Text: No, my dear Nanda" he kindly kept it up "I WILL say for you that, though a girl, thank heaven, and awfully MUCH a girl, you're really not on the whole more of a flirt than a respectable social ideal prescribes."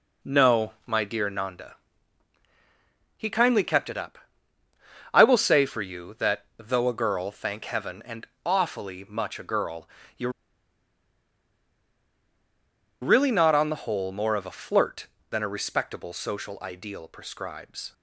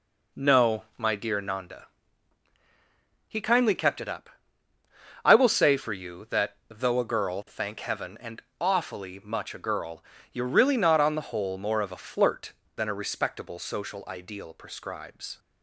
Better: second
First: pauses between "Nanda" and "he"; strong; at 1.7 s; 1.4 s long // pauses between "up" and "I"; noticeable; at 4.1 s; 0.92 s long // pauses between "and" and "awfully"; slight; at 8.2 s; 0.18 s long // pauses between "you're" and "really"; strong; at 10.2 s; 2.7 s long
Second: pauses between "Nanda" and "he"; strong; at 1.8 s; 1.4 s long // pauses between "up" and "I"; noticeable; at 4.3 s; 0.92 s long // pauses between "and" and "awfully"; slight; at 8.4 s; 0.18 s long

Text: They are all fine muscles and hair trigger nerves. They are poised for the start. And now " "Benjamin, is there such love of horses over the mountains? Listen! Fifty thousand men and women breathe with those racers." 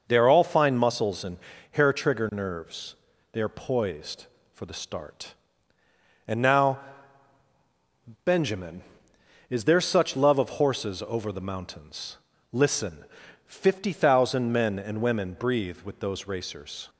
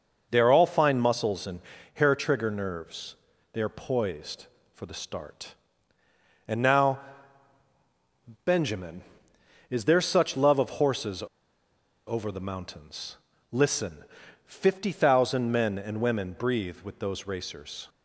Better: first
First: pauses between "and" and "hair"; slight; at 1.3 s; 0.34 s long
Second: pauses between "and" and "hair"; slight; at 1.5 s; 0.34 s long // pauses between "horses" and "over"; noticeable; at 11.2 s; 0.83 s long

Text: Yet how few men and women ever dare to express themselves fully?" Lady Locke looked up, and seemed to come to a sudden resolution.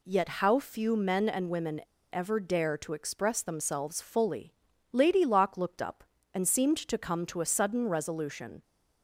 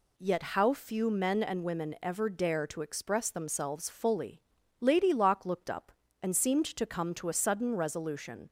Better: second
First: pauses between "women" and "ever"; slight; at 1.8 s; 0.30 s long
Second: none

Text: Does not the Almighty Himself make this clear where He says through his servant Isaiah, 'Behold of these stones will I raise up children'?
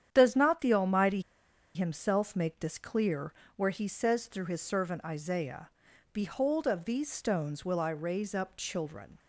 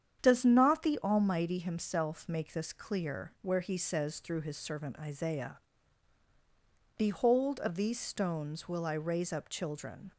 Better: second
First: starts louder than the rest; strong; until 1.1 s; 9.5 dB // pauses between "Almighty" and "Himself"; noticeable; at 1.2 s; 0.54 s long // pauses between "clear" and "where"; slight; at 3.3 s; 0.24 s long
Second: starts louder than the rest; strong; until 1.2 s; 8.5 dB

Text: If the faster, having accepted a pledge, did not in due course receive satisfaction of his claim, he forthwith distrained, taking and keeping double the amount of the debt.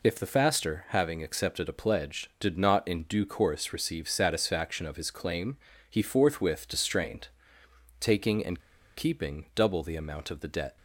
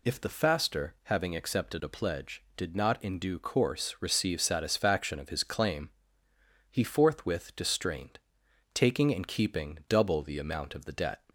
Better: second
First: pauses between "and" and "keeping"; at 8.5 s; 0.38 s long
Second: none

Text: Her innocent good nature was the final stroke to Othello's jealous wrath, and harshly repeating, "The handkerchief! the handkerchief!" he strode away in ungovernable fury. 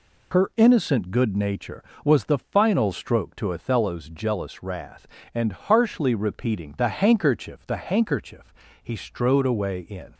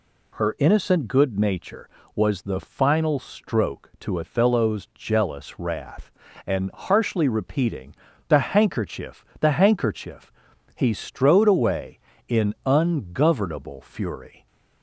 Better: second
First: stops before "ungovernable fury"; at 10.1 s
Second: none

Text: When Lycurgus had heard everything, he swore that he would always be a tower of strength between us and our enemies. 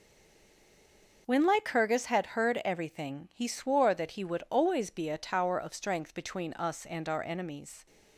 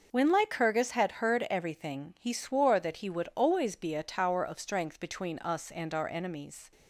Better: second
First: stays silent before the first word; noticeable; until 1.2 s; 1.2 s long // starts louder than the rest; noticeable; until 2.2 s; 6 dB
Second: starts louder than the rest; noticeable; until 1.1 s; 6 dB

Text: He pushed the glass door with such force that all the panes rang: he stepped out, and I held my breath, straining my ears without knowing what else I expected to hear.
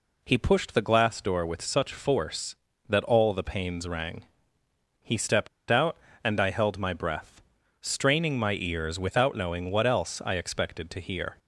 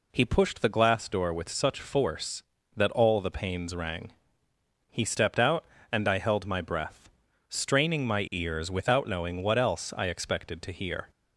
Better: second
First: pauses between "stepped" and "out"; slight; at 5.4 s; 0.21 s long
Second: none

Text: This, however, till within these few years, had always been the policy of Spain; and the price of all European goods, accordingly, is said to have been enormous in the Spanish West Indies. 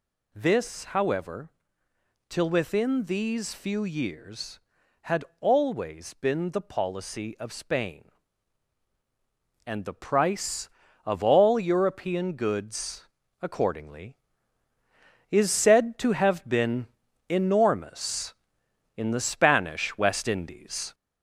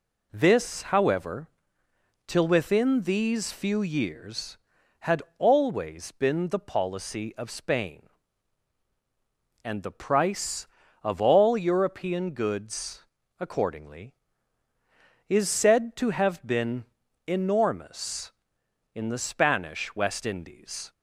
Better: second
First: gets louder; throughout; 3.5 dB // pauses between "had" and "always"; slight; at 5.2 s; 0.16 s long // pauses between "been" and "enormous"; at 16.8 s; 0.42 s long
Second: pauses between "had" and "always"; slight; at 5.2 s; 0.16 s long // pauses between "been" and "enormous"; at 16.8 s; 0.42 s long

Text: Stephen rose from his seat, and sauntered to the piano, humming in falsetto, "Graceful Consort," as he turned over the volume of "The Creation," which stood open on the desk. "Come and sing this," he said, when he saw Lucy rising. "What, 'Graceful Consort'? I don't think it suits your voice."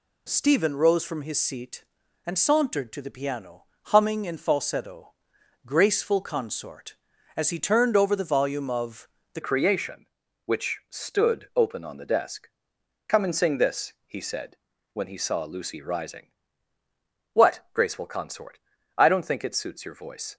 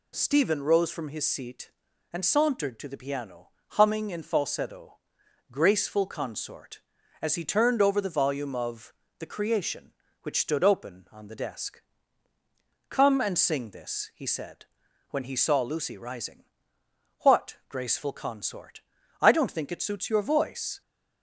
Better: second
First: pauses between "of" and "The"; slight; at 9.0 s; 0.24 s long // changes voice at "Creation"; from 9.4 s on; 10.9 s long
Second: pauses between "of" and "The"; slight; at 8.9 s; 0.24 s long

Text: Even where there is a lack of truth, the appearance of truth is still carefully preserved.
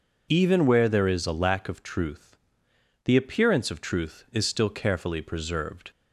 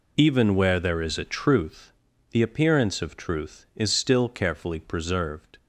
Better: first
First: none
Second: skips "lack of"; at 1.2 s

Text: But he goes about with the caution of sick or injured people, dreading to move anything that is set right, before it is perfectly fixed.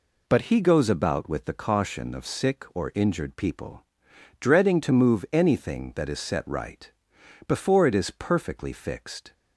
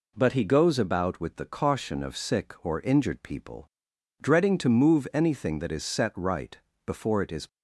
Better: first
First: none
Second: stops before "perfectly fixed"; at 7.4 s

